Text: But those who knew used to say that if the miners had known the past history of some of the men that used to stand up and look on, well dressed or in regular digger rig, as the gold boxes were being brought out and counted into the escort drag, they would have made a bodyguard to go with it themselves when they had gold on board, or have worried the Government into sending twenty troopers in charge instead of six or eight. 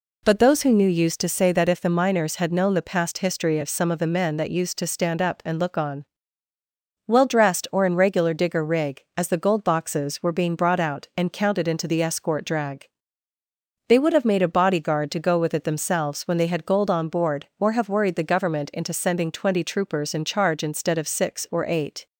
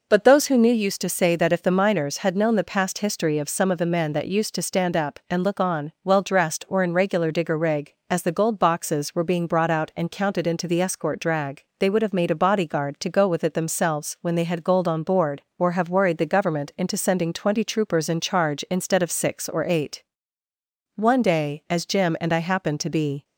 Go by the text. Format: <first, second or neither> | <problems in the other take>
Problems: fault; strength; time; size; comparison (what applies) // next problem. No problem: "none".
first | goes on to say "One day as Jim and I happened to be"; strong; from 20.9 s on; 2.2 s long